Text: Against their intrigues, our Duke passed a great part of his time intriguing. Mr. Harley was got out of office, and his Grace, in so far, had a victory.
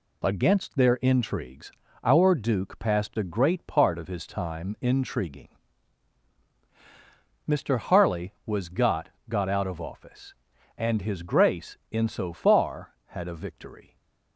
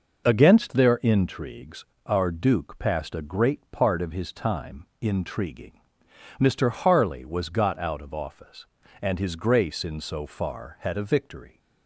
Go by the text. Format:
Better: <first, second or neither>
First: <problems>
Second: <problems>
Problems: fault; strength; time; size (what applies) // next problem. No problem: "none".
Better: second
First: says "got" twice; at 9.2 s // stays silent after the last word; slight; from 13.8 s on; 0.5 s long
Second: none